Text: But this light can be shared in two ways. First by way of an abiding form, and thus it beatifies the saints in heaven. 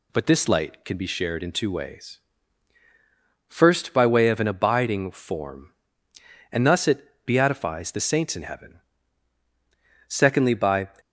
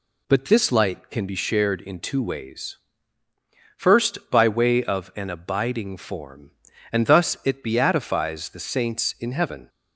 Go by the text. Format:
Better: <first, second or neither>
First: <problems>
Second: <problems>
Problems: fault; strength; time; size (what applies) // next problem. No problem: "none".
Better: second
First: pauses between "it" and "beatifies"; slight; at 7.0 s; 0.20 s long // goes on to say "Secondly by"; noticeable; from 10.0 s on; 0.80 s long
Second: none